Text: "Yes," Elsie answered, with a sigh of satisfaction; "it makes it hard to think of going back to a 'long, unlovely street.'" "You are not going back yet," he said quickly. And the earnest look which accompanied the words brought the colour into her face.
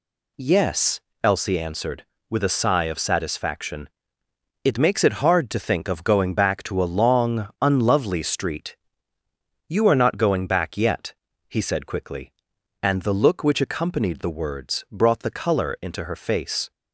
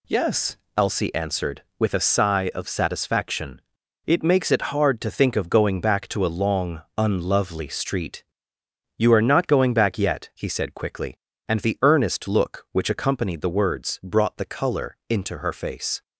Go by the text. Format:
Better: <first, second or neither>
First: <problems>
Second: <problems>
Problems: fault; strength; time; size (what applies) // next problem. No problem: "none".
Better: second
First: skips "earnest"; at 13.1 s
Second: none